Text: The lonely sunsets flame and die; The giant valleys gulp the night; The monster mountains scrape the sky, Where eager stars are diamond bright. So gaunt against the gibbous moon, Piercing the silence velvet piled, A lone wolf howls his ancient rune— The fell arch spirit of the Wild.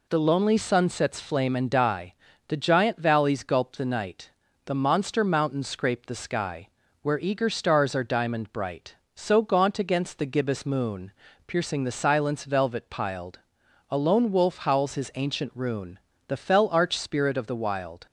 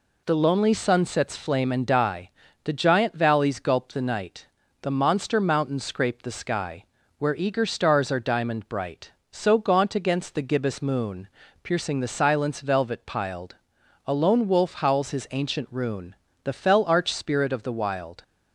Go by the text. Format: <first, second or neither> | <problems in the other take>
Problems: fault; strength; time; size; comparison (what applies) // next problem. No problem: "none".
neither | none